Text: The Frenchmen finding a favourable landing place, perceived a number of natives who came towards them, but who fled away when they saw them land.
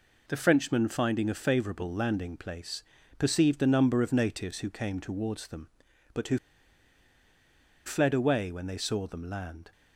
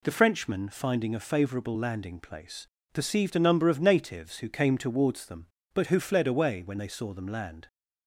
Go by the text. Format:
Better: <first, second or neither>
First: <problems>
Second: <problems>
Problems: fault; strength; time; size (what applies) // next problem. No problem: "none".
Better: second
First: pauses between "who" and "fled"; strong; at 6.3 s; 1.4 s long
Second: none